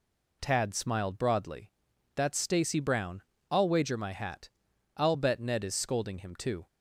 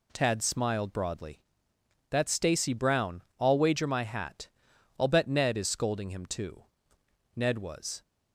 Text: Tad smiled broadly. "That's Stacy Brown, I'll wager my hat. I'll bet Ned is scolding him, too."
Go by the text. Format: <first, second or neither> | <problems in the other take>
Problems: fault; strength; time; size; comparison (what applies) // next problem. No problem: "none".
first | goes on to say "Ned was"; noticeable; from 7.3 s on; 0.66 s long